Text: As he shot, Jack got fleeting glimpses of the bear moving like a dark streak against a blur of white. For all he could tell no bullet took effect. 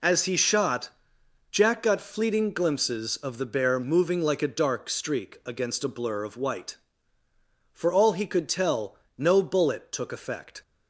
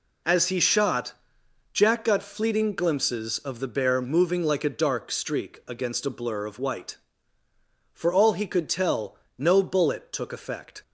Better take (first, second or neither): neither